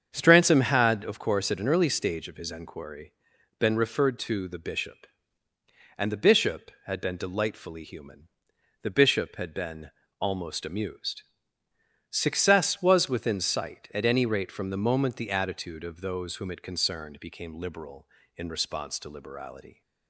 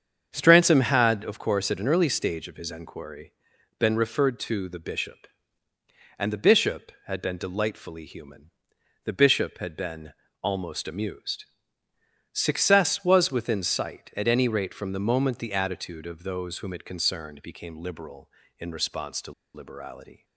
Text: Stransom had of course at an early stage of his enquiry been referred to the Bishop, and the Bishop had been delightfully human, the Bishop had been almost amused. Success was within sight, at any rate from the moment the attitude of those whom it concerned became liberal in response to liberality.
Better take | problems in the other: first | starts louder than the rest; strong; until 1.3 s; 7.5 dB; strong in the first // pauses between "enquiry" and "been"; noticeable; at 3.3 s; 0.46 s long; noticeable in the first // pauses between "been" and "almost"; slight; at 10.1 s; 0.30 s long; slight in the first // pauses between "to" and "liberality"; slight; at 19.3 s; 0.22 s long

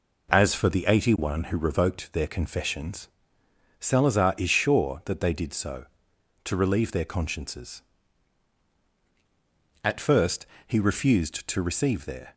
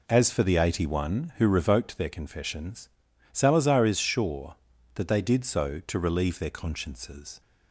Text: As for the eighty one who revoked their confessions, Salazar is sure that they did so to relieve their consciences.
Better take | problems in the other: second | goes on to say "At first he refused to receive their"; strong; from 9.8 s on; 2.5 s long

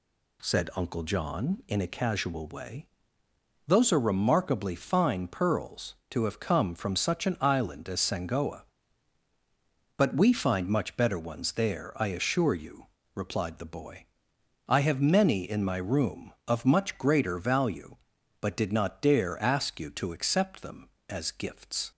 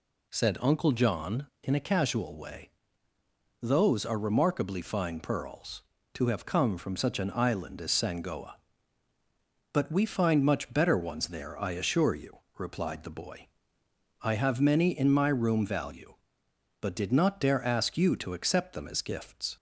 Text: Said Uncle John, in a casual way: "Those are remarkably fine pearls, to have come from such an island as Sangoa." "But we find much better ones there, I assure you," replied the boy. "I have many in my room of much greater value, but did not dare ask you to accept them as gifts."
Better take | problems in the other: first | skips "of much greater"; at 15.6 s

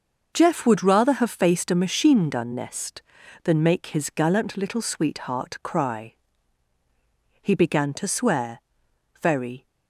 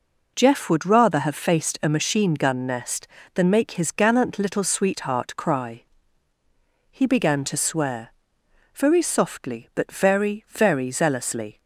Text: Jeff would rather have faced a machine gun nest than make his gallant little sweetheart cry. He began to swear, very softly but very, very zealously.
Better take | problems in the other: second | starts louder than the rest; noticeable; until 1.3 s; 6 dB // stops before "softly but very very zealously"; at 9.6 s

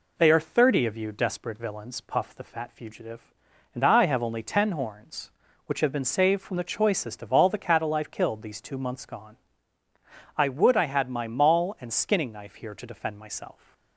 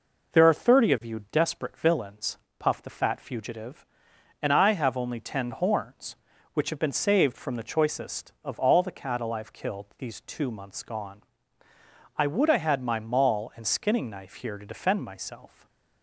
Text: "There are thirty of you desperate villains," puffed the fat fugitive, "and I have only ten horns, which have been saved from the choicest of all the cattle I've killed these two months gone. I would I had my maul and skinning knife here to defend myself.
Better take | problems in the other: second | says "They" for "There"; at 0.1 s

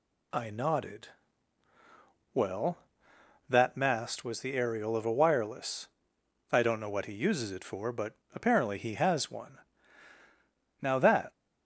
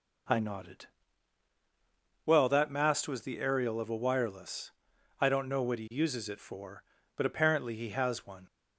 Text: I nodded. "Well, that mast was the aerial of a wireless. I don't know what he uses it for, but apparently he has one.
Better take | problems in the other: second | pauses between "but" and "apparently"; slight; at 8.1 s; 0.20 s long // goes on to say "Now that"; from 10.8 s on; 0.50 s long

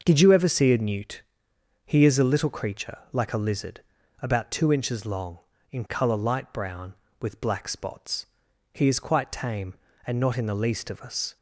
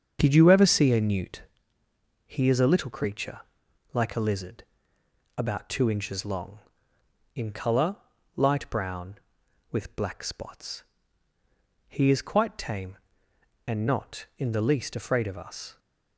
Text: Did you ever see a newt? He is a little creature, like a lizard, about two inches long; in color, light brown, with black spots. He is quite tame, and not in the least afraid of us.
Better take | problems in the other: second | starts louder than the rest; until 1.0 s; 6 dB; also in the second // skips "afraid"; at 10.9 s

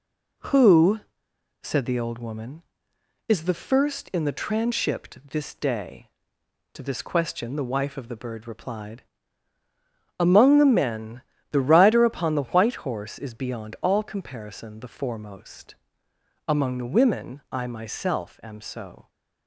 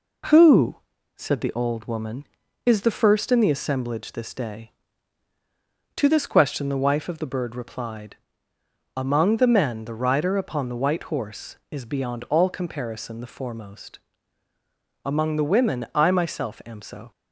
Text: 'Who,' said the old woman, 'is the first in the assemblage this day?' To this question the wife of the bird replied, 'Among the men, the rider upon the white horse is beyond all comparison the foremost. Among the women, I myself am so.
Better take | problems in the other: second | says "transhipped" for "assemblage"; at 4.3 s

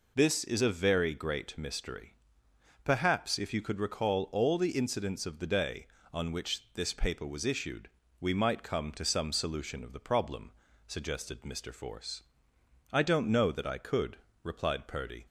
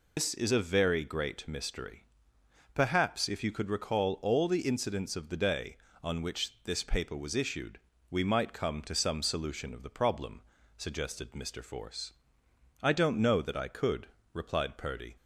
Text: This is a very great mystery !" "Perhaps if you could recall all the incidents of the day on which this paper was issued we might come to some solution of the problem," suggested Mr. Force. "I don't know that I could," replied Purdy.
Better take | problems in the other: first | loses the start of "This"; at 0.1 s; 110 ms // pauses between "issued" and "we"; slight; at 7.7 s; 0.32 s long; slight in the first

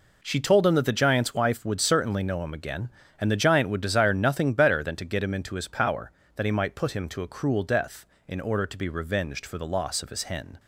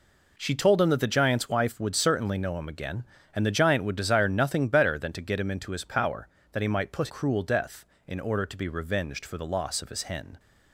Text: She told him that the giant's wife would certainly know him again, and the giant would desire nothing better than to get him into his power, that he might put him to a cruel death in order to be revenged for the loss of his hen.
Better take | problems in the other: first | skips "him to a"; at 7.0 s

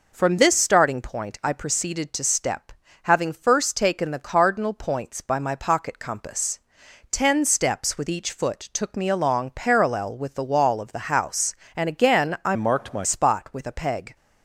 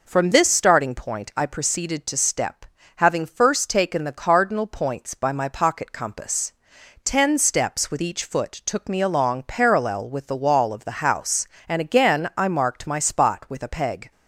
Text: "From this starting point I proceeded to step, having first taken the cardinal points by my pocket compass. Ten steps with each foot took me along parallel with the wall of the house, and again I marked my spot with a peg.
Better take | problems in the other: second | changes voice from "marked" to "my"; from 12.5 to 13.0 s; 0.5 s long

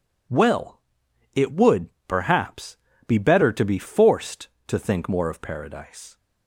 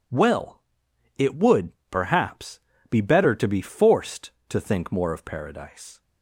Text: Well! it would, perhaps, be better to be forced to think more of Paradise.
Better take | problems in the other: neither | none

